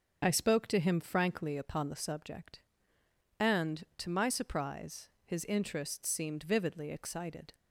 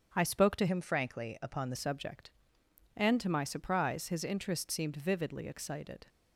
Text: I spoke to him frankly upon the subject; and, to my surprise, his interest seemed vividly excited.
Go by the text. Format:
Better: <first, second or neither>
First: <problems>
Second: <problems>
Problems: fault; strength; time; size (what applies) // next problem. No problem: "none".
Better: first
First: none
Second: starts louder than the rest; until 1.1 s; 7 dB // changes voice from "him" to "the"; from 0.6 to 1.7 s; 1.1 s long